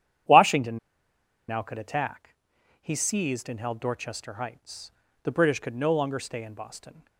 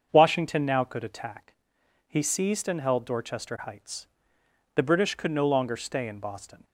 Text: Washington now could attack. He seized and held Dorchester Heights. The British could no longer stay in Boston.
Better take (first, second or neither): second